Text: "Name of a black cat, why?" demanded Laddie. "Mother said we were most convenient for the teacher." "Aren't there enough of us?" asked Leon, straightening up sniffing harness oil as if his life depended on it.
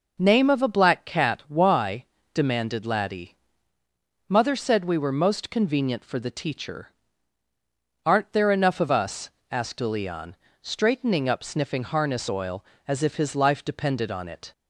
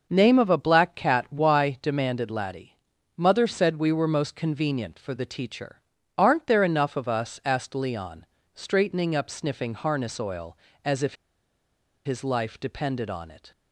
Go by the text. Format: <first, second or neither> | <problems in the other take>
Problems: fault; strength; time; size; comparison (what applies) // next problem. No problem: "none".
first | pauses between "if" and "his"; noticeable; at 11.1 s; 0.89 s long